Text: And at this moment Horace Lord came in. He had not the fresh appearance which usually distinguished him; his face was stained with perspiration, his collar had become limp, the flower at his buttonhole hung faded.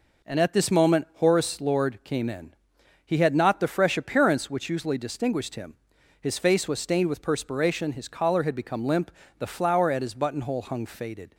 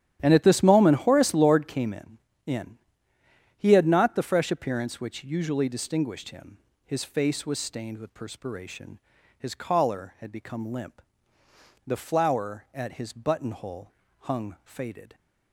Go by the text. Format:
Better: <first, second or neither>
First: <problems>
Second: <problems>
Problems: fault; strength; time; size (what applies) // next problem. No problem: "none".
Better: first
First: none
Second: starts louder than the rest; strong; until 1.2 s; 10.5 dB // says "in" twice; at 2.4 s // pauses between "buttonhole" and "hung"; slight; at 13.9 s; 0.26 s long